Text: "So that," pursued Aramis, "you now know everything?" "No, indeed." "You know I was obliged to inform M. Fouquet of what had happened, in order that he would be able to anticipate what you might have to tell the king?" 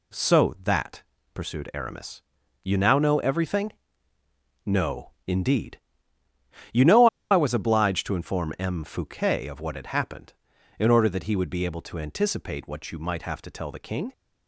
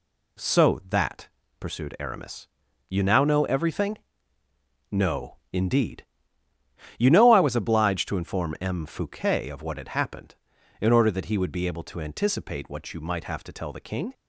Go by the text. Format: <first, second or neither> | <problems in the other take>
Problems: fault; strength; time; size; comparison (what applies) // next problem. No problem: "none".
second | pauses between "know" and "I"; slight; at 7.0 s; 0.24 s long